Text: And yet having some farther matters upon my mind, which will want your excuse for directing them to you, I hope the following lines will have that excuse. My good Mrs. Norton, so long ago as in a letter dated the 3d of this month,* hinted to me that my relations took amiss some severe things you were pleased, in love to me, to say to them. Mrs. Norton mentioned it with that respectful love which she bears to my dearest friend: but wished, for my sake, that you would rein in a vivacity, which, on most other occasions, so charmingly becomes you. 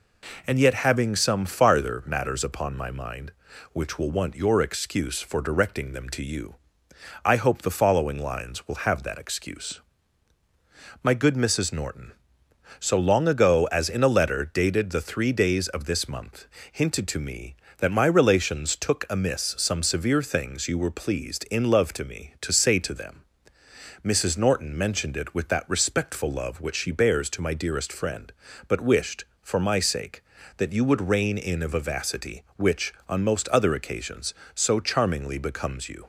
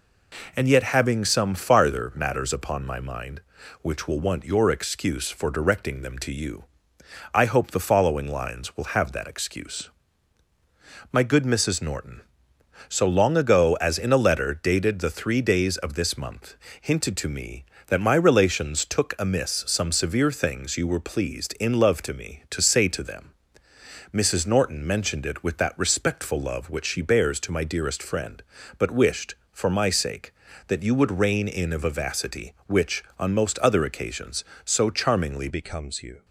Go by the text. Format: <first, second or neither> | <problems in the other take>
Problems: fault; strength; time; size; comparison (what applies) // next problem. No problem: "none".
first | changes voice at "becomes"; from 35.4 s on; 0.8 s long